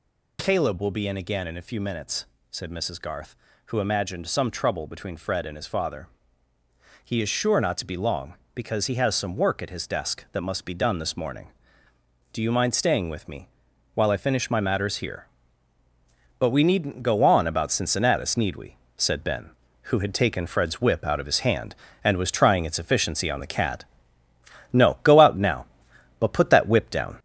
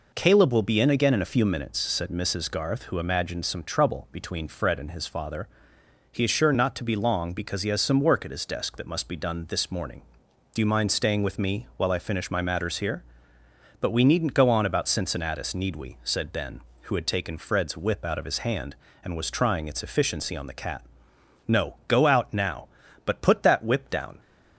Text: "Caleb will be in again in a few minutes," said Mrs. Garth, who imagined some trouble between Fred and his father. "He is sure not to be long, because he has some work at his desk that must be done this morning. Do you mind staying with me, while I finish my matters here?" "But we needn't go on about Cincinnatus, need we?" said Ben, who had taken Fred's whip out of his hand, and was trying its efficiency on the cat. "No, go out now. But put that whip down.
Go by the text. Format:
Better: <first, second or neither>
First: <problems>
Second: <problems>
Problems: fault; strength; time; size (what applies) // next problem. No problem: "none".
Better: second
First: gets louder; noticeable; throughout; 4.5 dB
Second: none